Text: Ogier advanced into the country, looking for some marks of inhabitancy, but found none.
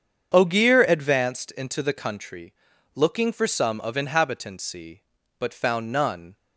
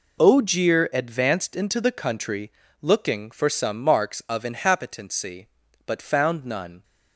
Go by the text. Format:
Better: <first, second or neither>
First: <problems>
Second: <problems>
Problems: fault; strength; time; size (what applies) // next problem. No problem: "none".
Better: second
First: starts louder than the rest; until 1.4 s; 7 dB // skips "marks"; at 3.8 s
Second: none